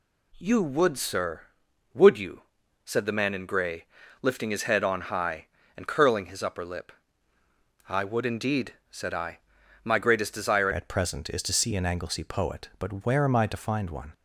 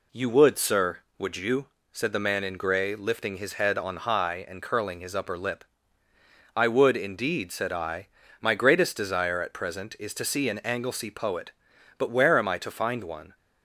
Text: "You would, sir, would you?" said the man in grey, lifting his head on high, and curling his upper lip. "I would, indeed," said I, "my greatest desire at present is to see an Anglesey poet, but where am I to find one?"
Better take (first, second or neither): second